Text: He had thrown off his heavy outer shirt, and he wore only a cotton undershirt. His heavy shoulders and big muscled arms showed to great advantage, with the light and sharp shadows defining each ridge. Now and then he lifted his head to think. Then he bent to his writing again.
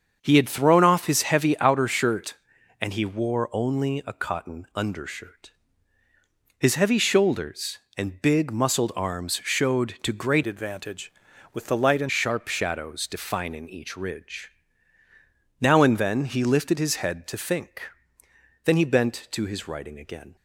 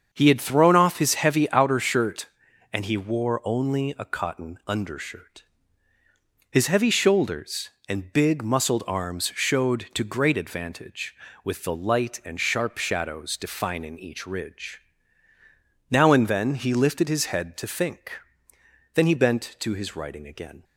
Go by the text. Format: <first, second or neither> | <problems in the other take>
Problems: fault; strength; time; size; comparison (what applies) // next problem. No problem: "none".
second | starts louder than the rest; strong; until 1.2 s; 7 dB; strong in the second // changes voice from "advantage" to "and"; from 10.4 to 12.1 s; 1.7 s long